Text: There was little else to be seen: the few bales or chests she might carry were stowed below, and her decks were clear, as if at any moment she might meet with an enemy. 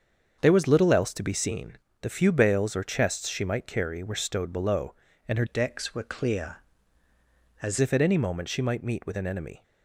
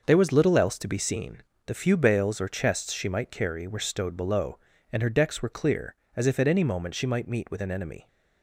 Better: second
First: starts louder than the rest; until 1.4 s; 7 dB // changes voice from "decks" to "as"; from 5.4 to 7.7 s; 2.3 s long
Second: starts louder than the rest; noticeable; until 1.0 s; 6 dB

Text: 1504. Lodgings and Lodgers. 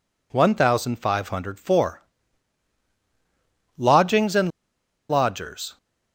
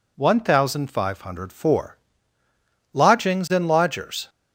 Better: second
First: pauses between "and" and "Lodgers"; noticeable; at 4.5 s; 0.59 s long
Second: none

